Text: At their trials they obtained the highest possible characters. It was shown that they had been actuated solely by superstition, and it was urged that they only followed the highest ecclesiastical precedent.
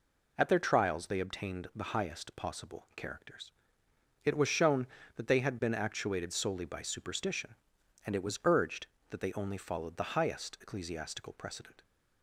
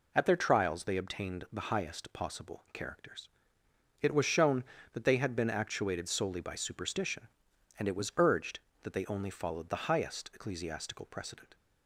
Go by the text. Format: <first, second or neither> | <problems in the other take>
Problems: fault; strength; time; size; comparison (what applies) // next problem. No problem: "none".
neither | none